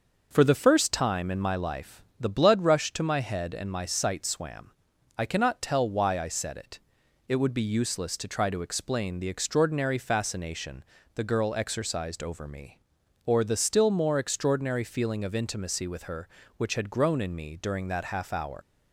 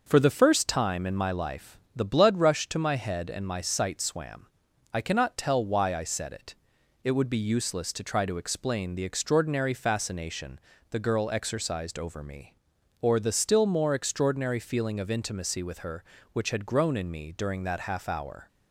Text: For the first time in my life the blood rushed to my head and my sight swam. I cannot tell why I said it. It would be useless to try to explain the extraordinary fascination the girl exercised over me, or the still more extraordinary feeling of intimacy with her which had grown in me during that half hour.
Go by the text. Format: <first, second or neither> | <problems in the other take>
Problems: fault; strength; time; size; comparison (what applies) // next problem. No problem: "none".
second | starts louder than the rest; until 1.3 s; 6.5 dB; also in the second // pauses between "life" and "the"; slight; at 2.0 s; 0.16 s long; slight in the second // pauses between "fascination" and "the"; slight; at 10.8 s; 0.30 s long; slight in the second // leaves "hour" unfinished; at 18.6 s; 100 ms